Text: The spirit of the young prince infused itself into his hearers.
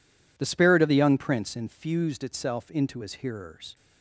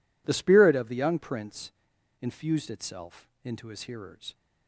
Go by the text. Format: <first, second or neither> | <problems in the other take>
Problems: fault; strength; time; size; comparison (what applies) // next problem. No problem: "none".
first | pauses between "prince" and "infused"; noticeable; at 1.7 s; 0.48 s long // pauses between "itself" and "into"; slight; at 3.2 s; 0.16 s long